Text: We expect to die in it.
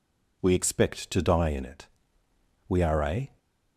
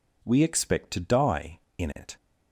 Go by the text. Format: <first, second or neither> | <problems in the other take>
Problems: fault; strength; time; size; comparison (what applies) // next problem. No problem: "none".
second | goes on to say "We are a"; noticeable; from 2.6 s on; 0.70 s long